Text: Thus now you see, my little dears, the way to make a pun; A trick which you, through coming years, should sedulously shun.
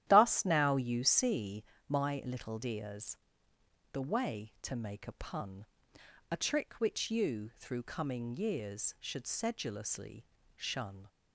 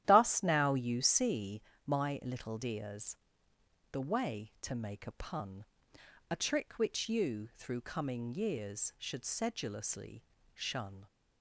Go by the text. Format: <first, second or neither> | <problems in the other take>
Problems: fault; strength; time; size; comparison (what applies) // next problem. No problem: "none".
neither | starts louder than the rest; strong; the same in both // pauses between "sedulously" and "shun"; slight; the same in both